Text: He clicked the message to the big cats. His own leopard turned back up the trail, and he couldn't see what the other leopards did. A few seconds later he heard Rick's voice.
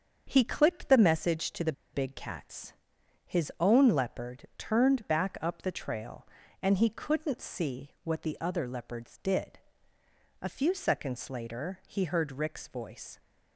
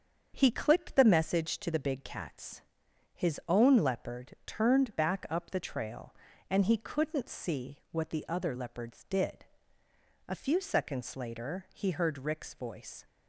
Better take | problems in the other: second | starts louder than the rest; until 1.3 s; 7 dB; strong in the second // pauses between "the" and "big"; slight; at 1.7 s; 0.21 s long

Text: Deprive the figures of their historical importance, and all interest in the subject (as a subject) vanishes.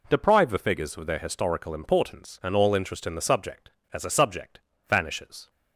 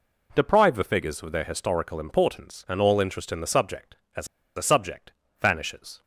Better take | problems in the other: first | pauses between "as" and "a"; slight; at 4.2 s; 0.30 s long

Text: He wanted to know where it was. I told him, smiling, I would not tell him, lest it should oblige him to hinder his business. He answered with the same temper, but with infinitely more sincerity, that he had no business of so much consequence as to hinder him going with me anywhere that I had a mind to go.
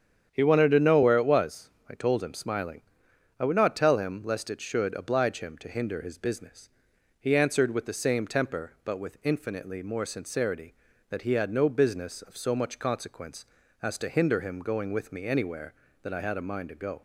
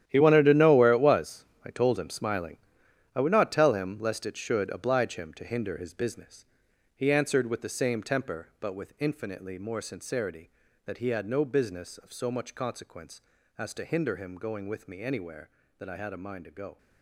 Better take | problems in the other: first | gets quieter; strong; throughout; 13 dB // starts louder than the rest; strong; until 1.1 s; 11 dB; strong in the first

